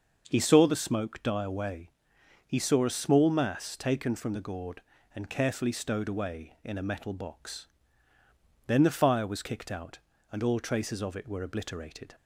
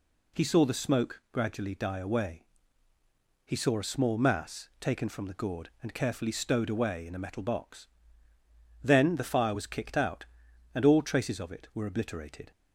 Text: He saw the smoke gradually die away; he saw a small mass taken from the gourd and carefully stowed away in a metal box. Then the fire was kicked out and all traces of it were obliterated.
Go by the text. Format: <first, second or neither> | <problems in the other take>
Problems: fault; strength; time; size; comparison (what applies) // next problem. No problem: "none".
second | starts louder than the rest; until 1.2 s; 6 dB // skips "gradually"; at 1.2 s